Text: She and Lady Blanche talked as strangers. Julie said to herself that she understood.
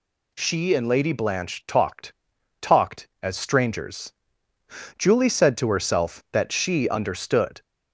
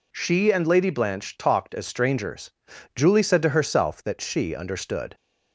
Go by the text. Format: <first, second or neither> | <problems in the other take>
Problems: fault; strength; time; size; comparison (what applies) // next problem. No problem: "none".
second | says "talked" twice; at 2.6 s